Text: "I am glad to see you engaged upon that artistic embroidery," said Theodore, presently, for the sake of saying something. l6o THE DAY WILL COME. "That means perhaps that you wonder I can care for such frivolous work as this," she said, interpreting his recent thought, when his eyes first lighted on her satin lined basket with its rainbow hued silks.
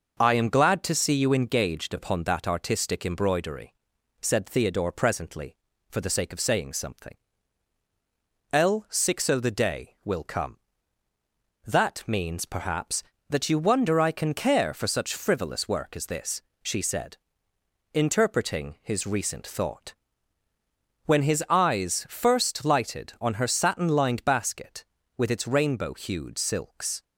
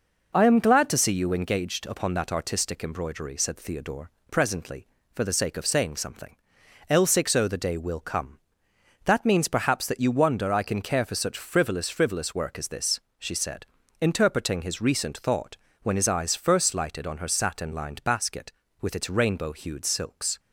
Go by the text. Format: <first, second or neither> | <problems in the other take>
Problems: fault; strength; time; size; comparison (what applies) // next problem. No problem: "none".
first | says "frivolous" twice; at 11.9 s